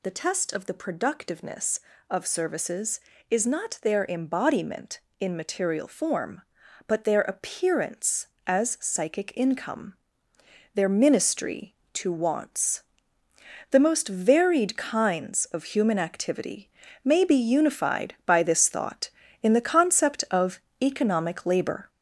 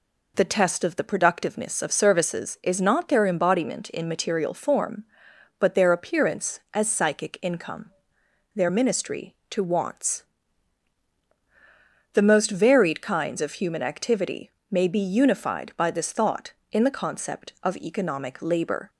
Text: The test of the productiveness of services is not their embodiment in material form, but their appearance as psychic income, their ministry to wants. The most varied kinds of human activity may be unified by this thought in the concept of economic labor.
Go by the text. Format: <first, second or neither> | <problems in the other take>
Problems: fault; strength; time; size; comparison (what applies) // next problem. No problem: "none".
second | gets louder; noticeable; throughout; 5 dB // pauses between "activity" and "may"; slight; at 16.6 s; 0.34 s long; slight in the second // pauses between "of" and "economic"; slight; at 20.5 s; 0.22 s long